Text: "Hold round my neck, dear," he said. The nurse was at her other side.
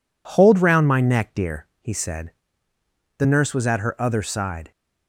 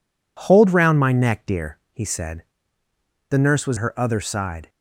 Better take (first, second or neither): first